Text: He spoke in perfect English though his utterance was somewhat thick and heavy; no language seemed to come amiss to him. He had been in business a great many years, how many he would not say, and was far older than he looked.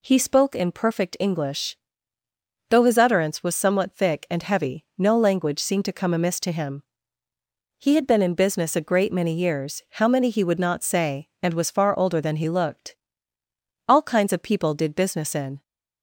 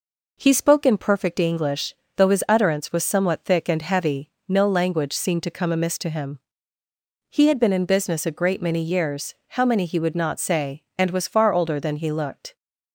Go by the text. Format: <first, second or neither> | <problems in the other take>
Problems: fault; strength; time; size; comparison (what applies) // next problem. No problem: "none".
second | pauses between "English" and "though"; noticeable; at 1.7 s; 0.92 s long; slight in the second // goes on to say "All kinds of people did business in"; strong; from 13.8 s on; 1.7 s long